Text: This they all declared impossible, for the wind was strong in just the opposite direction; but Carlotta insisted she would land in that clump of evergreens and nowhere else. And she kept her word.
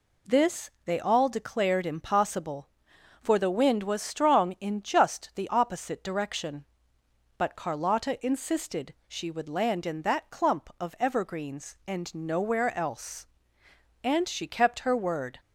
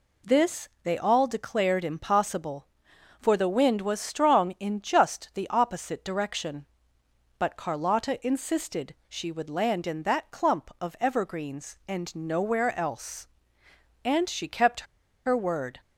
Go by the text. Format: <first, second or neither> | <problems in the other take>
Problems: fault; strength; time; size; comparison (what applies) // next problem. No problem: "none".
first | pauses between "kept" and "her"; at 14.8 s; 0.41 s long